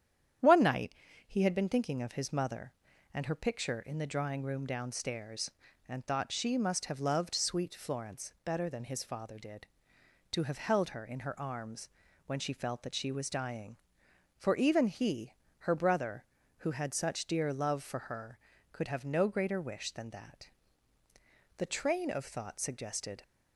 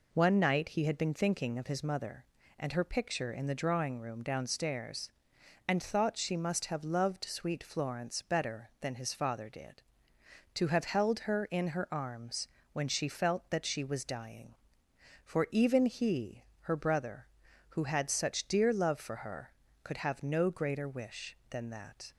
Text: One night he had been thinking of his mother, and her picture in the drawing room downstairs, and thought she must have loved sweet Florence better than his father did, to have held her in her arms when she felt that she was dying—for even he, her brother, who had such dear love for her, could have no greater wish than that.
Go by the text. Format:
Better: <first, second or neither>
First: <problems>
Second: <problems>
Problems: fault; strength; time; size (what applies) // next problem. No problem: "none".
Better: second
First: starts louder than the rest; strong; until 1.7 s; 9.5 dB // pauses between "night" and "he"; slight; at 0.9 s; 0.32 s long // pauses between "arms" and "when"; at 11.8 s; 0.38 s long // goes on to say "The train of thought suggested"; from 21.5 s on; 1.6 s long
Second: pauses between "arms" and "when"; slight; at 12.4 s; 0.24 s long